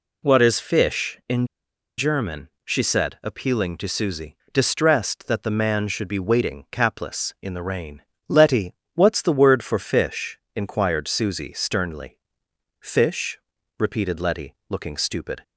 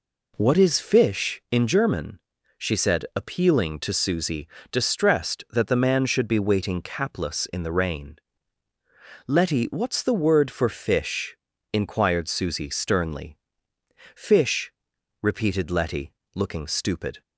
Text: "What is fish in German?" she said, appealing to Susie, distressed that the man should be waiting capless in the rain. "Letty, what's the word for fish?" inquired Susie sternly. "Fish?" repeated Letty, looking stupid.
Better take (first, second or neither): second